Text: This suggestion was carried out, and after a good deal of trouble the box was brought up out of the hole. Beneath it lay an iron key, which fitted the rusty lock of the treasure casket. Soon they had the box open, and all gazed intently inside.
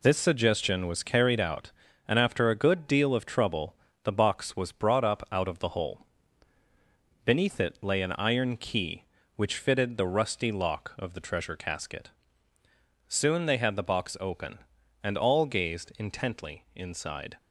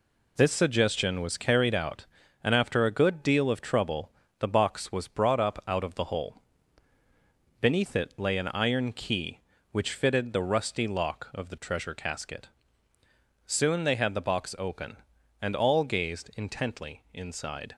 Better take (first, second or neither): neither